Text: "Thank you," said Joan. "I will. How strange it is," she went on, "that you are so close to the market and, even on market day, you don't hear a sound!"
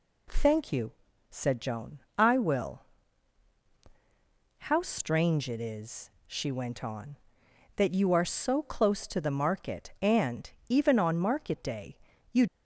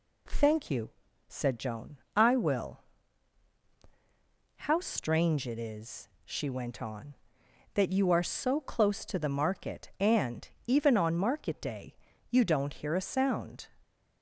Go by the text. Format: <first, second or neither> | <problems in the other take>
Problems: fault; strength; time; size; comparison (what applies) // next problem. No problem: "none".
second | stops before "don't hear a sound"; at 12.4 s